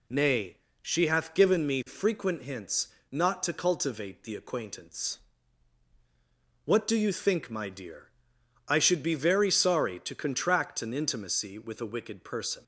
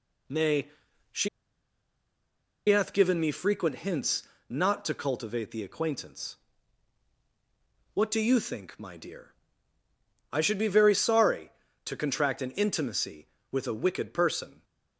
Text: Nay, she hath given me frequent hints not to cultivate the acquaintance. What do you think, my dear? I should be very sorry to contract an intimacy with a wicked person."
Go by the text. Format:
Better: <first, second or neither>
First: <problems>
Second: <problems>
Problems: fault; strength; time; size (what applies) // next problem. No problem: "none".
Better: first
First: pauses between "hints" and "not"; slight; at 2.8 s; 0.22 s long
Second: pauses between "she" and "hath"; strong; at 1.2 s; 1.4 s long // pauses between "hints" and "not"; slight; at 4.2 s; 0.26 s long